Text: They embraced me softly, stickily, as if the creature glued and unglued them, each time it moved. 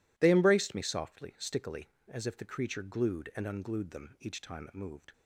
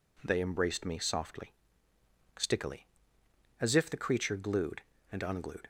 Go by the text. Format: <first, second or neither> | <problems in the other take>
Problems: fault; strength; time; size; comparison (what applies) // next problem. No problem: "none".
first | stops before "them each time it moved"; at 5.6 s